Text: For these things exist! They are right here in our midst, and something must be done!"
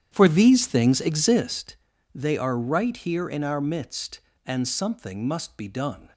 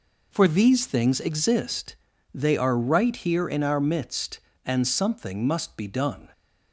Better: second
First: starts louder than the rest; strong; until 1.6 s; 9.5 dB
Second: none

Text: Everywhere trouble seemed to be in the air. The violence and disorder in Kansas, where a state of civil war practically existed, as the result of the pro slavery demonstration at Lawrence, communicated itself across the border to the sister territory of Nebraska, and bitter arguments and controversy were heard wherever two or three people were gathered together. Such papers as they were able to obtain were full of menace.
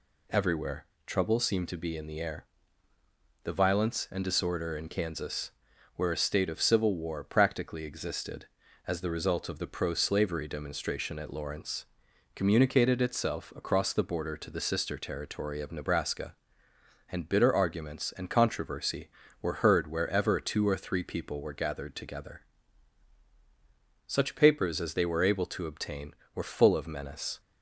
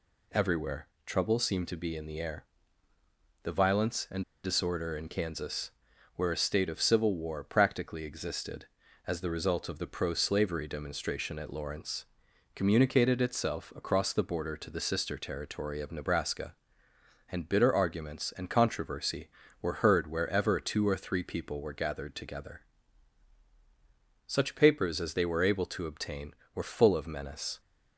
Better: first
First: pauses between "Everywhere" and "trouble"; slight; at 0.8 s; 0.20 s long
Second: pauses between "Everywhere" and "trouble"; slight; at 0.8 s; 0.18 s long // pauses between "and" and "disorder"; slight; at 4.2 s; 0.22 s long

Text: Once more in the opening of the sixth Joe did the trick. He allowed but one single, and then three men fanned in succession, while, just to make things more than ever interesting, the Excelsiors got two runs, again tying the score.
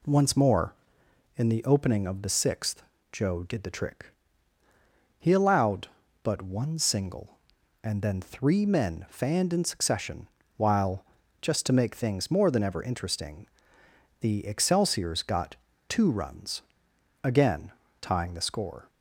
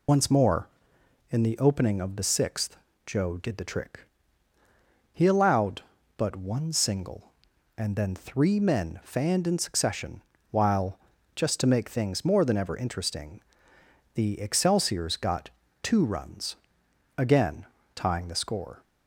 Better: first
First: pauses between "sixth" and "Joe"; slight; at 2.8 s; 0.30 s long // pauses between "got" and "two"; slight; at 15.5 s; 0.32 s long // pauses between "again" and "tying"; slight; at 17.7 s; 0.30 s long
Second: loses the start of "Once"; at 0.0 s; 125 ms // pauses between "sixth" and "Joe"; slight; at 2.7 s; 0.30 s long // pauses between "got" and "two"; slight; at 15.4 s; 0.32 s long // pauses between "again" and "tying"; slight; at 17.6 s; 0.30 s long

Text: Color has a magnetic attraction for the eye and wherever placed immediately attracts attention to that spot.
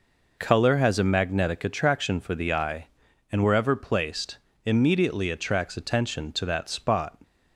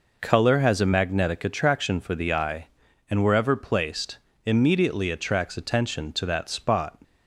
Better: neither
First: pauses between "placed" and "immediately"; slight; at 4.3 s; 0.30 s long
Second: pauses between "placed" and "immediately"; slight; at 4.1 s; 0.30 s long

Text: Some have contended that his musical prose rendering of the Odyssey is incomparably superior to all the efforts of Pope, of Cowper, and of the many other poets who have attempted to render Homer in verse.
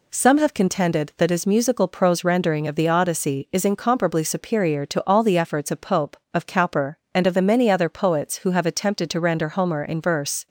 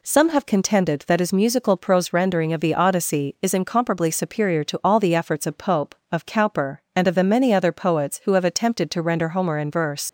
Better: first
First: none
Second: leaves "verse" unfinished; at 10.0 s; 90 ms

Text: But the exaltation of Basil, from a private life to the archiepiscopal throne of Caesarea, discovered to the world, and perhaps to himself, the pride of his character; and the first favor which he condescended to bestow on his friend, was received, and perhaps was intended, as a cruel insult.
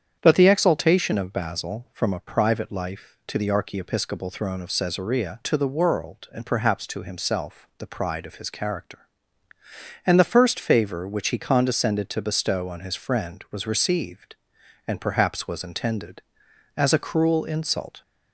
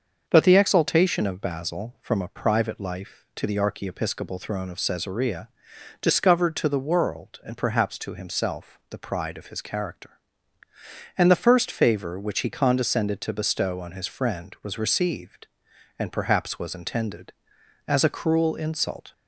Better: second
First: starts louder than the rest; strong; until 1.2 s; 8.5 dB // skips "discovered"; at 5.4 s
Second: starts louder than the rest; until 1.2 s; 6.5 dB

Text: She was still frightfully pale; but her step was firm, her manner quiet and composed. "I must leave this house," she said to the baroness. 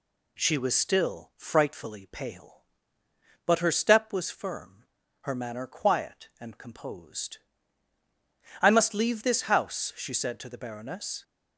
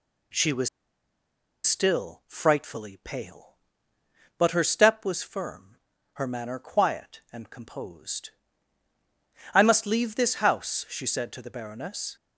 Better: first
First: none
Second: pauses between "was" and "still"; noticeable; at 0.6 s; 0.97 s long

